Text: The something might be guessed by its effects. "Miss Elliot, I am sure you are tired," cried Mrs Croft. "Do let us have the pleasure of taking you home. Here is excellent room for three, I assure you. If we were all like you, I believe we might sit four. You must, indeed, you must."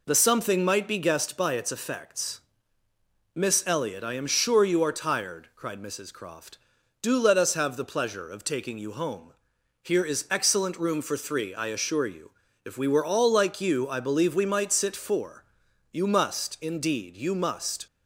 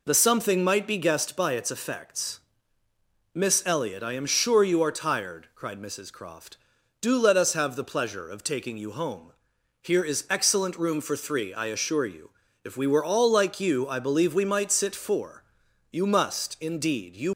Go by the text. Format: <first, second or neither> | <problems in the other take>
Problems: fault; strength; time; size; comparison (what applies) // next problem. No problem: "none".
first | stops before "must"; at 17.3 s